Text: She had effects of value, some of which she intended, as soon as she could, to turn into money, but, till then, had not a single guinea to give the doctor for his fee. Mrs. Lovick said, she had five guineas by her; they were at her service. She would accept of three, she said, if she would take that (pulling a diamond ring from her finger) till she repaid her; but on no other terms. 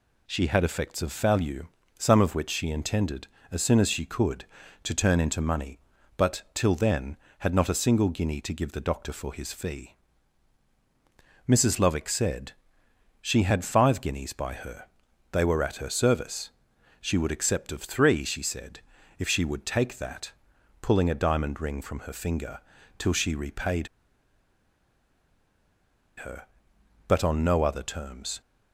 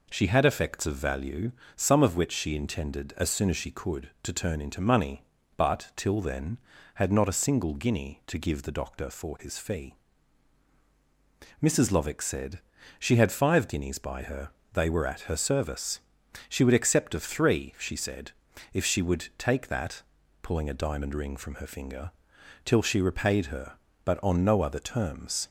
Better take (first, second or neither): second